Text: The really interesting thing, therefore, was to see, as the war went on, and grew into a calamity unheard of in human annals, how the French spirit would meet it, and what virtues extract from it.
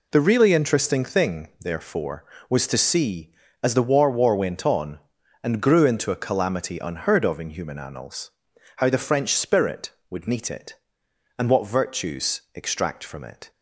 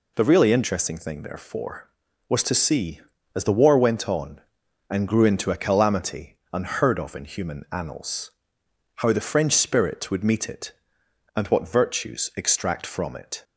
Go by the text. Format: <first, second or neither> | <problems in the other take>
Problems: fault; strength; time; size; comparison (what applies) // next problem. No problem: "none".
second | says "war" twice; at 4.0 s